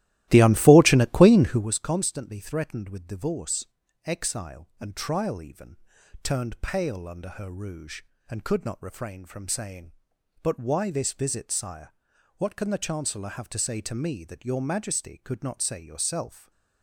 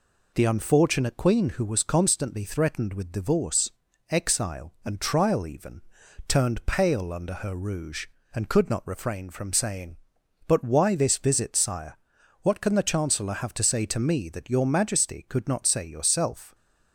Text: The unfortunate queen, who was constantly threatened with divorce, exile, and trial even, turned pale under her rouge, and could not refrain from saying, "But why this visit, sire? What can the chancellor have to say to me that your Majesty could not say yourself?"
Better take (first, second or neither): second